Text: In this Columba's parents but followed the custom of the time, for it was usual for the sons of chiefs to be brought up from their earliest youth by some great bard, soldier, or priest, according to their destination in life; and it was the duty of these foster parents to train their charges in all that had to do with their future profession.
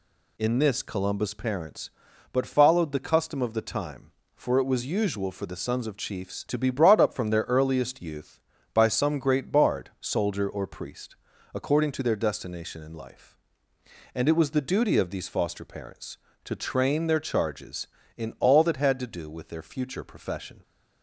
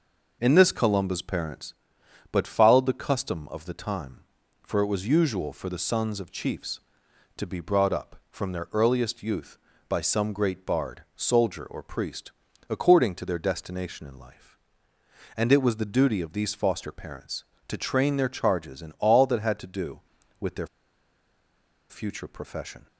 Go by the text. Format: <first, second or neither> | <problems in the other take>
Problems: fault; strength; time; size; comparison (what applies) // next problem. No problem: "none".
first | pauses between "their" and "future"; at 20.6 s; 1.2 s long